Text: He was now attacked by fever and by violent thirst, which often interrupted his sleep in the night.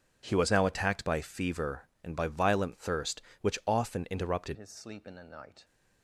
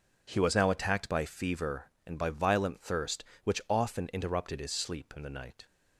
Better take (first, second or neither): second